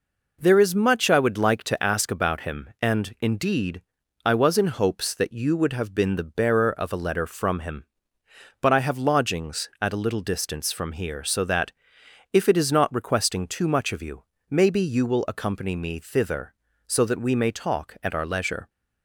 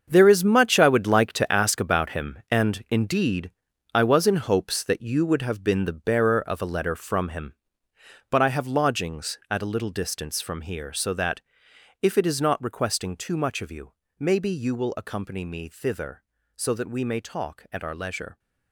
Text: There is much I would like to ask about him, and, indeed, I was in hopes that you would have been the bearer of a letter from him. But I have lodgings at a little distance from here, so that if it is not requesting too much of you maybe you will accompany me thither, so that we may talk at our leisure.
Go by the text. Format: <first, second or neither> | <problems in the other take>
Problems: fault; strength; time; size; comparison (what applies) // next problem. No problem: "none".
first | gets quieter; strong; throughout; 11.5 dB // pauses between "that" and "if"; noticeable; at 11.4 s; 0.58 s long; noticeable in the first // pauses between "you" and "maybe"; slight; at 13.9 s; 0.28 s long; slight in the first